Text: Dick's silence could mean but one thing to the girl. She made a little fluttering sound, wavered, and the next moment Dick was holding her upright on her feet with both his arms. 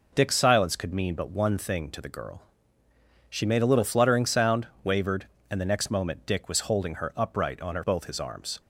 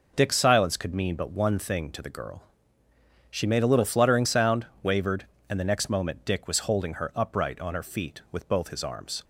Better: second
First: skips "feet with"; at 7.8 s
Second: none

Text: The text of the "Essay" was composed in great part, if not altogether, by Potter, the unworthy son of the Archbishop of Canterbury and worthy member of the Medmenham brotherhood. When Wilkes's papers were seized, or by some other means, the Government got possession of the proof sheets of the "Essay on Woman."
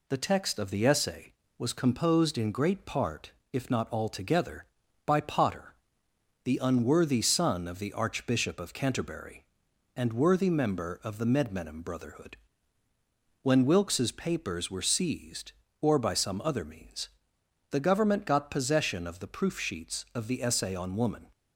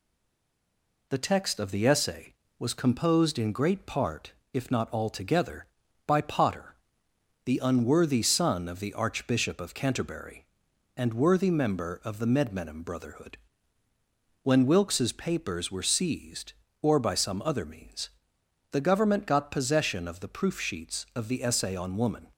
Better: first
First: none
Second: stays silent before the first word; until 1.0 s; 1.0 s long

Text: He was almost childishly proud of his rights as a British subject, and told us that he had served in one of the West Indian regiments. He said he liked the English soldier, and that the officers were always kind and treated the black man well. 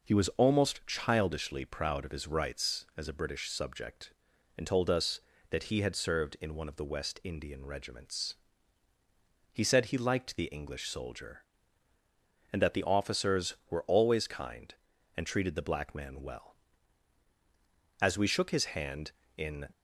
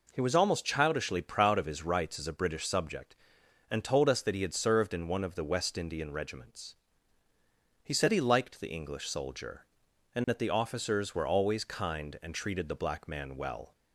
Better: second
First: goes on to say "As we shook his hand in"; from 18.0 s on; 1.6 s long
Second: none

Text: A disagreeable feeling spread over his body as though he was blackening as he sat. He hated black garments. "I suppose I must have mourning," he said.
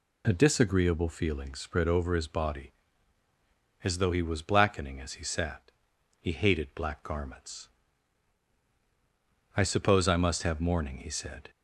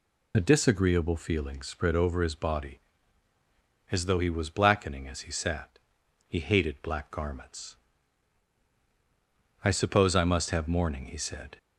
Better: first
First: none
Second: loses the start of "A"; at 0.3 s; 25 ms

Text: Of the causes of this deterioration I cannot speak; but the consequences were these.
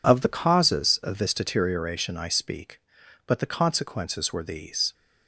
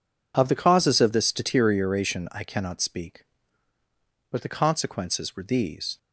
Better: second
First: skips "cannot"; at 2.2 s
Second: none

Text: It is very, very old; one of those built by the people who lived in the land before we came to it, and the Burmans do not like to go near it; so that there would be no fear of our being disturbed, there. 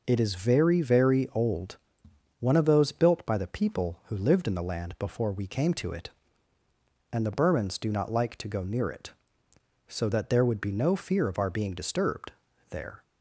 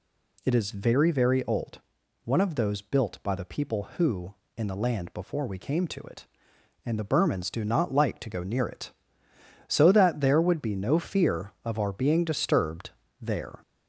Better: first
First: none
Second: skips "lived"; at 4.4 s

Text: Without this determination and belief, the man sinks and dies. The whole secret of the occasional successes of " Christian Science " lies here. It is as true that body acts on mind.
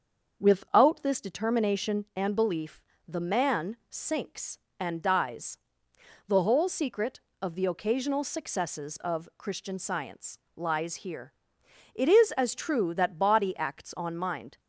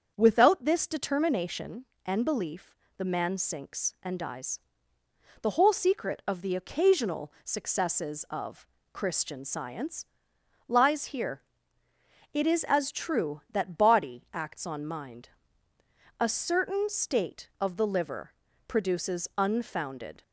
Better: first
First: starts louder than the rest; until 1.3 s; 6.5 dB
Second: starts louder than the rest; strong; until 1.1 s; 7 dB // goes on to say "A certain state of the liver produces unfounded"; strong; from 16.2 s on; 4.0 s long

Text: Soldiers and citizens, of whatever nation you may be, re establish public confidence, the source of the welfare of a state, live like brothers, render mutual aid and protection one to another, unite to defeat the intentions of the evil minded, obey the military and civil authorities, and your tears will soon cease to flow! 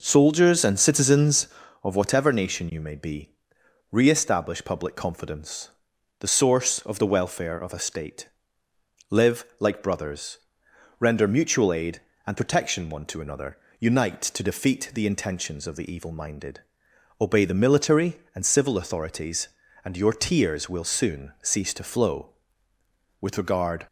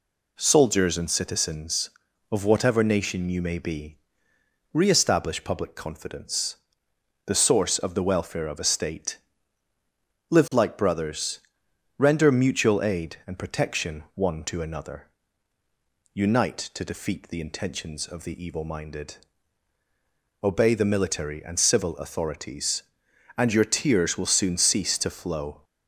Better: second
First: pauses between "live" and "like"; slight; at 9.4 s; 0.16 s long // goes on to say "With regard"; noticeable; from 23.2 s on; 0.66 s long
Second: none

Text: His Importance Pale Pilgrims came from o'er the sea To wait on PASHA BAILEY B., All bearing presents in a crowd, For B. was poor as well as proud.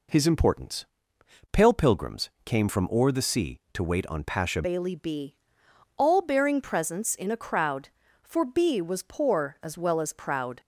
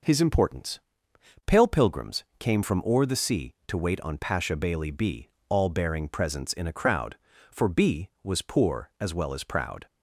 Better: second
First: pauses between "Importance" and "Pale"; noticeable; at 0.8 s; 0.66 s long // changes voice at "BAILEY"; from 4.6 s on; 6.0 s long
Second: pauses between "Importance" and "Pale"; noticeable; at 0.7 s; 0.66 s long

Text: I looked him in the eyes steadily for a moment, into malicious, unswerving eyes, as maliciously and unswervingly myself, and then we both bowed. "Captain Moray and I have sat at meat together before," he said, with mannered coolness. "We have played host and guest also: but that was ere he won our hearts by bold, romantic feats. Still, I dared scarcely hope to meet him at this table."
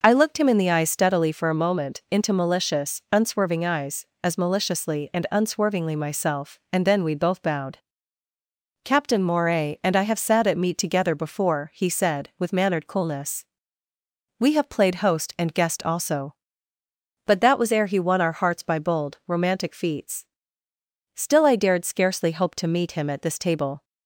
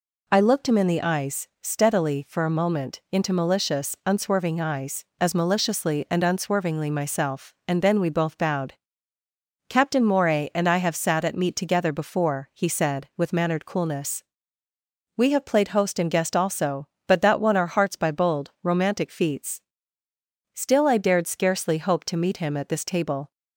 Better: first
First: none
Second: skips "was ere he"; at 17.3 s

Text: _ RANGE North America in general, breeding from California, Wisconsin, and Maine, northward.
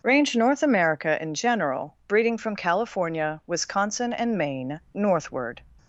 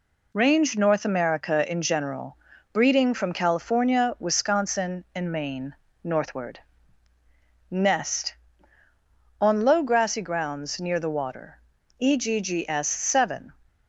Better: first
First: none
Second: goes on to say "NEST On low grassy grounds near the water EGGS Seven"; strong; from 7.6 s on; 5.8 s long

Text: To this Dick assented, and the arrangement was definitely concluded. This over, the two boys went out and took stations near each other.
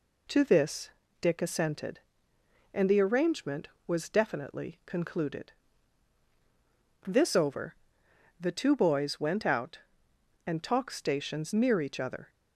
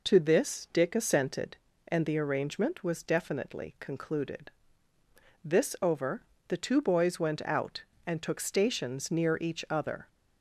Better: second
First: pauses between "this" and "Dick"; slight; at 0.8 s; 0.32 s long // says "talk" for "took"; at 10.6 s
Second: none

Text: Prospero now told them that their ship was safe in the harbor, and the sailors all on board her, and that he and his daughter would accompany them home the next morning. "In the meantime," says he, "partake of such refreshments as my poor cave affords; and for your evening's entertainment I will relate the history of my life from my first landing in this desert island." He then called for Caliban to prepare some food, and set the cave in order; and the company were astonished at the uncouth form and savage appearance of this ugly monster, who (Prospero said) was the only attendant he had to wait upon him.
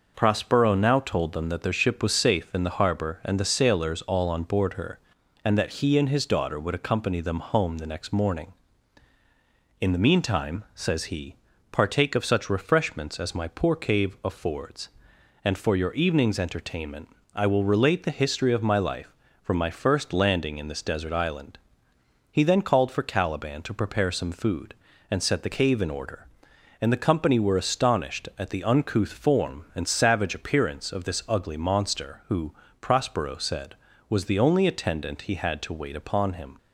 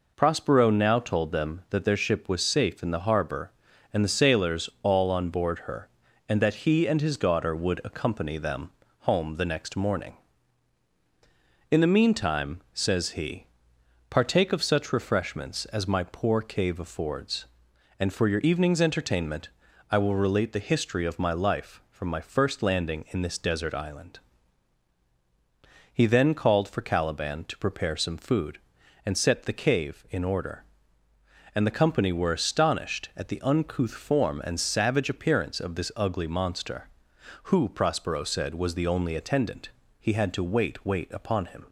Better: first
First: pauses between "entertainment" and "I"; slight; at 17.0 s; 0.24 s long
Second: pauses between "them" and "home"; slight; at 8.6 s; 0.30 s long // pauses between "entertainment" and "I"; at 19.4 s; 0.42 s long // pauses between "attendant" and "he"; slight; at 39.6 s; 0.30 s long // says "wait" twice; at 40.8 s

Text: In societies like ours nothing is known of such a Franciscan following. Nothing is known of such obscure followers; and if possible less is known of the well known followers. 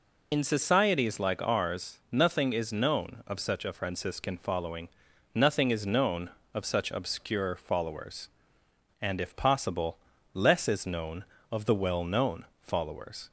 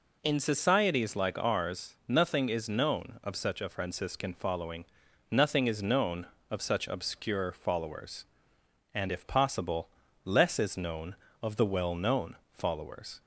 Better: second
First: loses the start of "In"; at 0.3 s; 70 ms // pauses between "possible" and "less"; slight; at 9.9 s; 0.36 s long // pauses between "known" and "followers"; slight; at 12.4 s; 0.16 s long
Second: pauses between "possible" and "less"; slight; at 9.8 s; 0.36 s long // pauses between "known" and "followers"; slight; at 12.3 s; 0.16 s long

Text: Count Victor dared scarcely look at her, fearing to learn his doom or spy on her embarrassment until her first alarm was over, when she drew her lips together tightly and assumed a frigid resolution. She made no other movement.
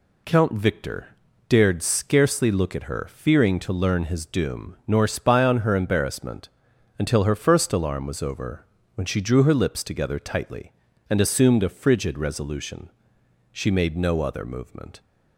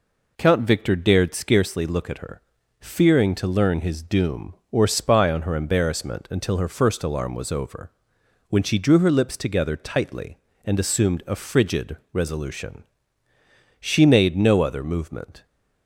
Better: second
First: pauses between "Victor" and "dared"; at 1.0 s; 0.40 s long // says "nor" for "or"; at 4.8 s // pauses between "embarrassment" and "until"; noticeable; at 6.4 s; 0.50 s long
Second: none

